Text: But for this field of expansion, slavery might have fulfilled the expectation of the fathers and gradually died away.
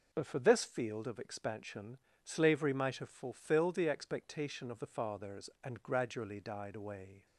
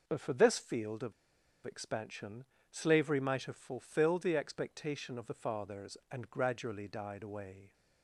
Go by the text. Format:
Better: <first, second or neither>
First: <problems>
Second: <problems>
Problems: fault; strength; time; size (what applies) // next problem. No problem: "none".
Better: first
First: none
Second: pauses between "of" and "expansion"; noticeable; at 1.1 s; 0.53 s long